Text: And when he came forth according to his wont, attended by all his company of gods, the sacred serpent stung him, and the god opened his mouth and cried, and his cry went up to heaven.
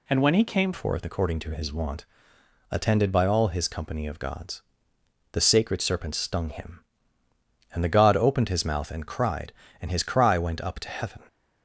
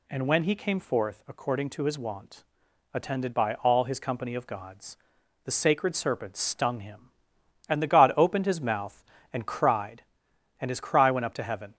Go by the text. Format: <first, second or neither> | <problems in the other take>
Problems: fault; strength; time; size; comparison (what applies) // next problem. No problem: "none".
second | changes voice at "forth"; from 0.7 s on; 10.5 s long